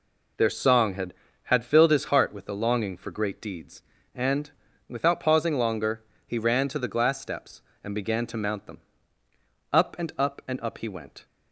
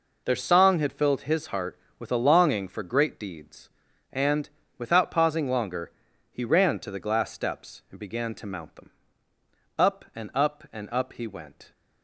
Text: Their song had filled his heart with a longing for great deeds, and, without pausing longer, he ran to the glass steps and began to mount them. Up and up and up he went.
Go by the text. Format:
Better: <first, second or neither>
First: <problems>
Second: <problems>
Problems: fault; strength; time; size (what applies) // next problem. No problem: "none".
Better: second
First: says "had" twice; at 1.4 s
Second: none